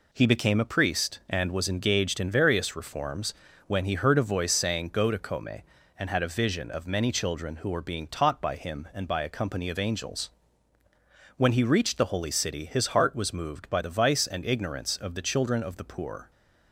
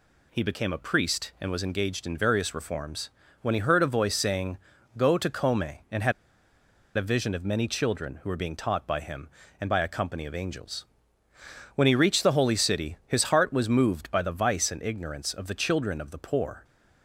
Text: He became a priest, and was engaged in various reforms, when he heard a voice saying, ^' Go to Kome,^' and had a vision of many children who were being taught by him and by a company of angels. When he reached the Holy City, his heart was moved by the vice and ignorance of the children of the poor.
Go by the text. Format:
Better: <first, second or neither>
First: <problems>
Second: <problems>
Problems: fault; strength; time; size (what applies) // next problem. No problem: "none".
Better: first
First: none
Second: pauses between "had" and "a"; noticeable; at 6.1 s; 0.83 s long